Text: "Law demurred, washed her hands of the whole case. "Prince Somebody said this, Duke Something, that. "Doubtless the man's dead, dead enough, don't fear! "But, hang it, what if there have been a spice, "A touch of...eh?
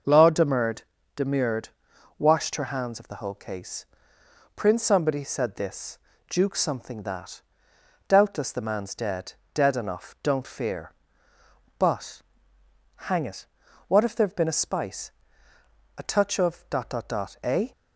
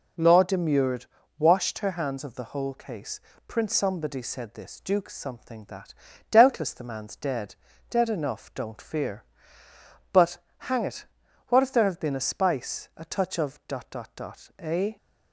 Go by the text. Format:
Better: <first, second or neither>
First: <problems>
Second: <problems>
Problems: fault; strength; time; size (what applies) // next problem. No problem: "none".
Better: second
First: says "demurred" twice; at 1.1 s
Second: none